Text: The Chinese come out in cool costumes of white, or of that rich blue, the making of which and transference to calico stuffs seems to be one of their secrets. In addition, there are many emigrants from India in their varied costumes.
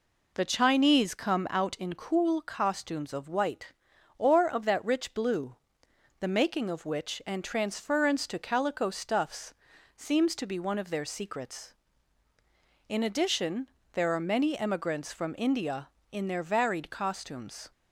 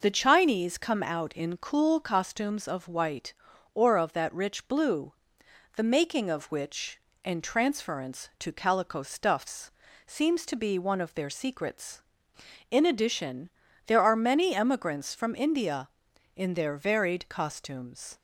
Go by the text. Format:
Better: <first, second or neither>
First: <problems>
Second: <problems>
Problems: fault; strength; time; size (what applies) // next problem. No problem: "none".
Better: neither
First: pauses between "stuffs" and "seems"; at 9.5 s; 0.44 s long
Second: pauses between "stuffs" and "seems"; at 9.6 s; 0.38 s long